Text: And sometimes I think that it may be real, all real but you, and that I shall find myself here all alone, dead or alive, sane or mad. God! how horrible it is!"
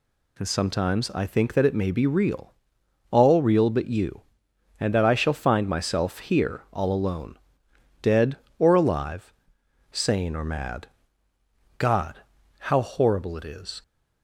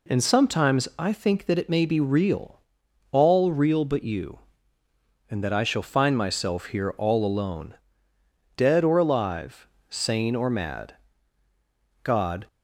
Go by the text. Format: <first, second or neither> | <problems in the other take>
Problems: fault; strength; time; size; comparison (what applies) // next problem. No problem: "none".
first | stops before "how horrible it is"; at 12.4 s